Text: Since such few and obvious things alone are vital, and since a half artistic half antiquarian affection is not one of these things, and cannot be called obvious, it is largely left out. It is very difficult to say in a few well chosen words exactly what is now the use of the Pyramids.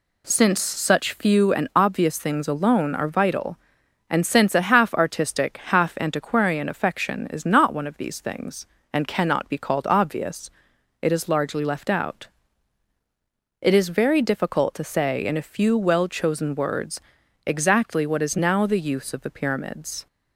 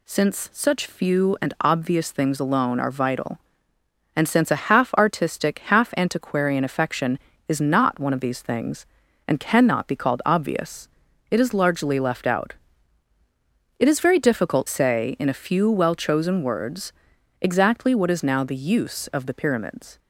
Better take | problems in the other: first | skips "to"; at 14.6 s // pauses between "words" and "exactly"; noticeable; at 16.9 s; 0.48 s long; also in the first

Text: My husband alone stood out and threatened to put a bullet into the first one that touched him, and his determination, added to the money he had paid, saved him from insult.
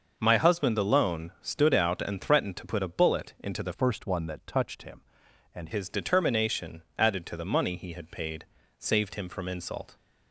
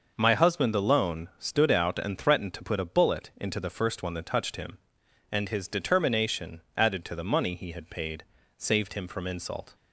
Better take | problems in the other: second | starts louder than the rest; noticeable; until 1.1 s; 6 dB // changes voice from "first" to "and"; from 3.7 to 5.6 s; 1.9 s long

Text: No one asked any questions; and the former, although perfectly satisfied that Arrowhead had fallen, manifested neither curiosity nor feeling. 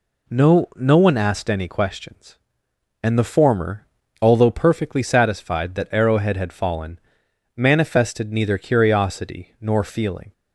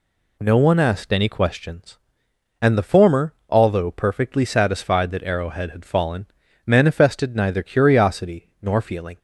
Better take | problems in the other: second | says "No" twice; at 0.7 s

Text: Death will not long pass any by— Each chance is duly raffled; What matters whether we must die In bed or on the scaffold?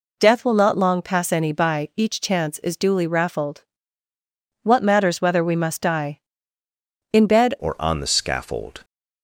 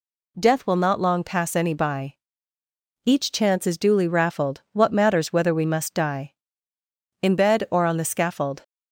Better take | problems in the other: second | changes voice at "or"; from 7.5 s on; 1.3 s long

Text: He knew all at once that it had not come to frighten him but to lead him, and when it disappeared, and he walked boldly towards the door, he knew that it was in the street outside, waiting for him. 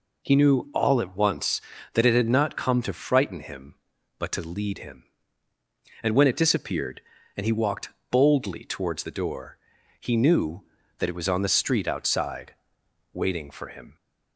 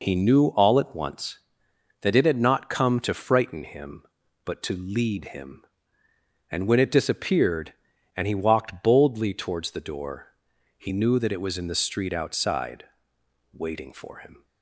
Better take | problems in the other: second | pauses between "walked" and "boldly"; slight; at 7.8 s; 0.20 s long // says "on" for "in"; at 11.2 s

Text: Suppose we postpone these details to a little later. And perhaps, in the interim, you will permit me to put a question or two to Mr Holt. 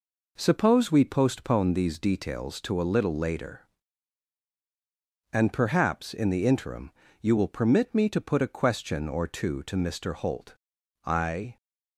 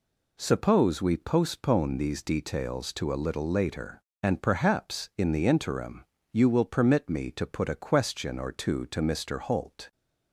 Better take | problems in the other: second | goes on to say "I"; from 11.0 s on; 0.50 s long

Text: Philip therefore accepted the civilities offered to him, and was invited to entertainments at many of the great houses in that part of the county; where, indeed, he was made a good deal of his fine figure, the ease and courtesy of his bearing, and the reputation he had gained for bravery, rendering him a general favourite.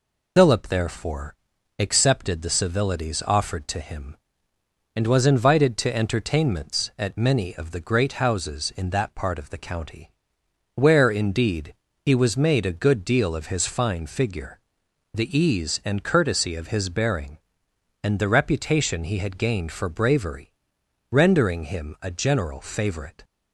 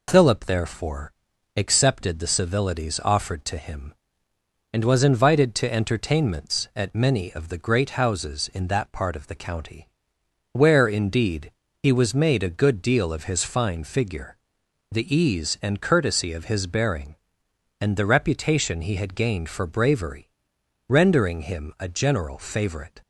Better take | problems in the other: second | loses the start of "Philip"; at 0.3 s; 55 ms // pauses between "therefore" and "accepted"; at 1.3 s; 0.42 s long; also in the second

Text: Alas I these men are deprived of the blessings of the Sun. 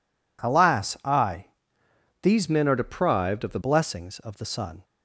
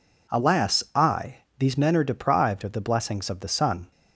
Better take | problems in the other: second | pauses between "I" and "these"; noticeable; at 1.4 s; 0.76 s long; slight in the second // changes voice from "men" to "the"; from 2.4 to 3.5 s; 1.1 s long

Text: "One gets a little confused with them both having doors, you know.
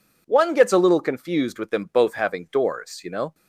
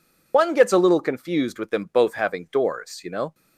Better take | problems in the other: first | loses the start of "One"; at 0.3 s; 85 ms

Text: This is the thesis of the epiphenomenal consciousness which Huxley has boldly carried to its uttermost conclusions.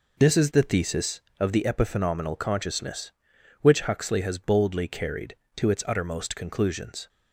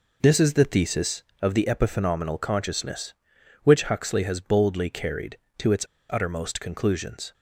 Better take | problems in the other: first | pauses between "its" and "uttermost"; slight; at 5.8 s; 0.24 s long

